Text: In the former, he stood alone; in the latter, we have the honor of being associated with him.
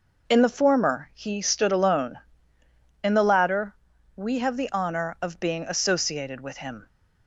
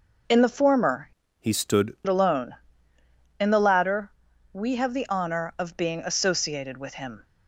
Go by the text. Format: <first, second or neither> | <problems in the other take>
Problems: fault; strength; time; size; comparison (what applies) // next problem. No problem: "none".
first | changes voice from "he" to "stood"; from 1.3 to 1.9 s; 0.6 s long